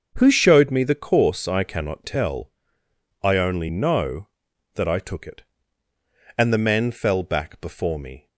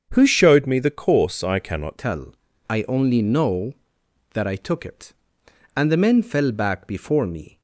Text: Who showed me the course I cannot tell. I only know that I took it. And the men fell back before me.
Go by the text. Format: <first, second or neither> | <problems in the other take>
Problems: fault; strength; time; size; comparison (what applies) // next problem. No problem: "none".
first | starts louder than the rest; until 1.1 s; 7 dB; also in the first // changes voice at "tell"; from 1.9 s on; 5.6 s long